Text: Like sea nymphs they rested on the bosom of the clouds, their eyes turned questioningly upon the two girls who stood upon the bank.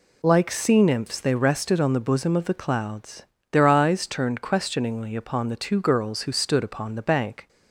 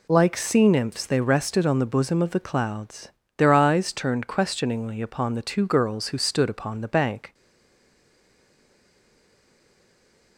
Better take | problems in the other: first | stays silent after the last word; strong; from 7.3 s on; 3.0 s long

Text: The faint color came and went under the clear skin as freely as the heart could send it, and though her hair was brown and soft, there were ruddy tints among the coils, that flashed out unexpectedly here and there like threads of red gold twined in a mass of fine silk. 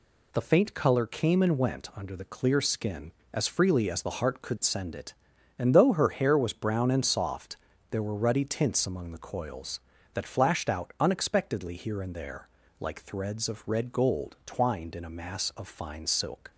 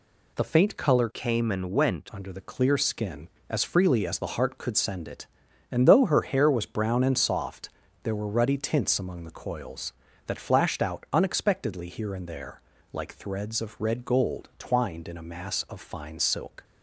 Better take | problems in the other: first | changes voice from "came" to "went"; from 1.1 to 2.0 s; 0.9 s long // pauses between "there" and "like"; slight; at 12.6 s; 0.32 s long; slight in the first

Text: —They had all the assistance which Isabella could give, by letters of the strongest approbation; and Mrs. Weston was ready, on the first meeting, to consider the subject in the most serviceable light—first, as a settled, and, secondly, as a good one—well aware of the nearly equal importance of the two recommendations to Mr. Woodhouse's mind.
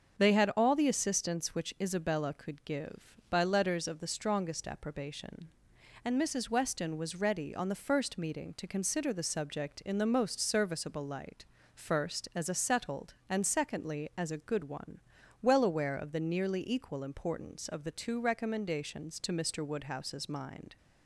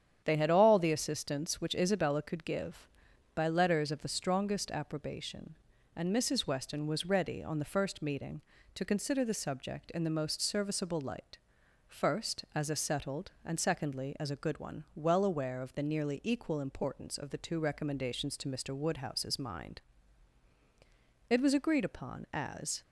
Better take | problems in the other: first | starts louder than the rest; strong; until 1.2 s; 9 dB; also in the first // goes on to say "It was agreed upon as"; from 21.3 s on; 1.5 s long

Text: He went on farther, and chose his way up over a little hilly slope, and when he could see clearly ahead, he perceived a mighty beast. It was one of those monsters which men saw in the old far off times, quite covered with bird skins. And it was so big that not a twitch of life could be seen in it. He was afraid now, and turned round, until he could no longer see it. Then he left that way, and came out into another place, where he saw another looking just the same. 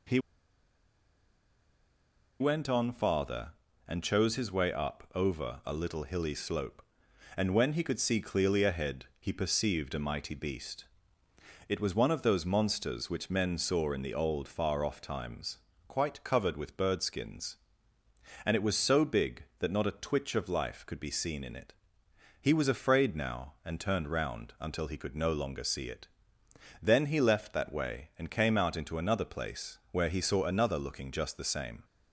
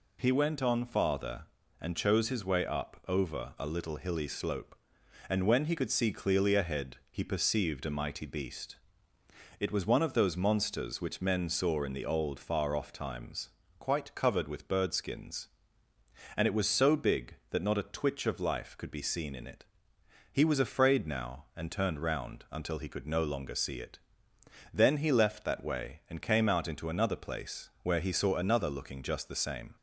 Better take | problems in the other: second | pauses between "He" and "went"; strong; at 0.1 s; 2.2 s long

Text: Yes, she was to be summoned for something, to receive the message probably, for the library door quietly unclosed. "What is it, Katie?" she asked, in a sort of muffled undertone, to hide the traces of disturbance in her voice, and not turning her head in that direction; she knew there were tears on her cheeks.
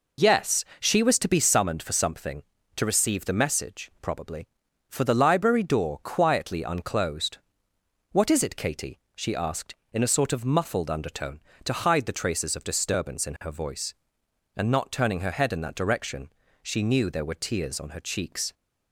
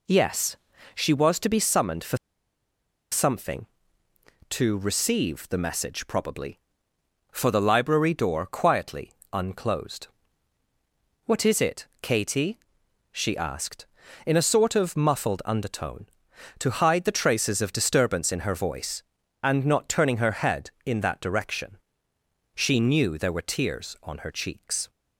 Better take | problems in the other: first | pauses between "for" and "something"; noticeable; at 2.1 s; 0.94 s long // pauses between "quietly" and "unclosed"; slight; at 9.1 s; 0.20 s long

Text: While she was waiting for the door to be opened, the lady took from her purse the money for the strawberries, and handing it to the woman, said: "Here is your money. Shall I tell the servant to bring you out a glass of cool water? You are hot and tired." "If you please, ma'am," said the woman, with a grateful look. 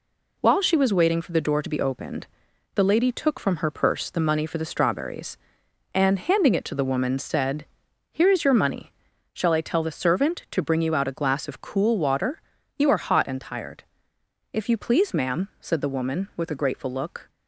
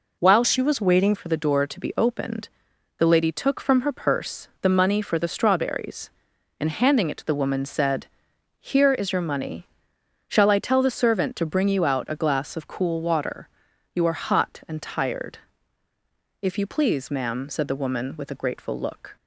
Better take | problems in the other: first | changes voice from "she" to "waiting"; from 0.4 to 1.1 s; 0.7 s long // pauses between "purse" and "the"; slight; at 4.4 s; 0.16 s long

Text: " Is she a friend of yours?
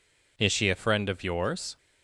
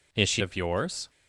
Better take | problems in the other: first | skips "a friend"; at 0.4 s

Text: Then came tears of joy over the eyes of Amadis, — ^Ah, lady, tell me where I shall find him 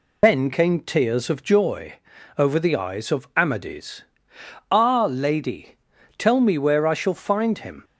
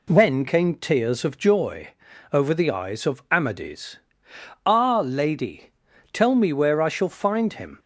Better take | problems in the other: second | loses the start of "Then"; at 0.2 s; 105 ms // pauses between "joy" and "over"; at 1.9 s; 0.44 s long; also in the second

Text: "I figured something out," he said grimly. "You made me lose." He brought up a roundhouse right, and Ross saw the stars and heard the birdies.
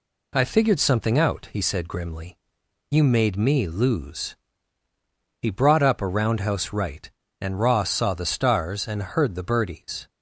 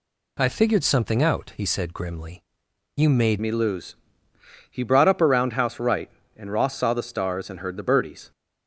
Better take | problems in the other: first | changes voice at "me"; from 3.4 s on; 4.9 s long

